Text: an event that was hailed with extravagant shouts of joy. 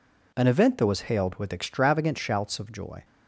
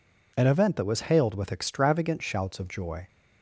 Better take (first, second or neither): neither